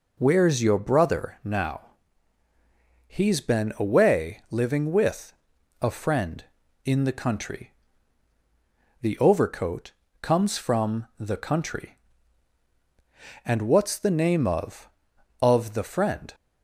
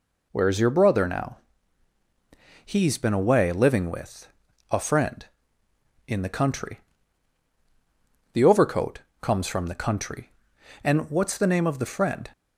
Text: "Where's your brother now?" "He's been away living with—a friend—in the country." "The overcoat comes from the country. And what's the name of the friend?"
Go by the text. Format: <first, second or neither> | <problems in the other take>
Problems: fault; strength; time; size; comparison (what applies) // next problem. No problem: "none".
second | pauses between "overcoat" and "comes"; slight; at 9.9 s; 0.28 s long; slight in the second // says "of" twice; at 15.4 s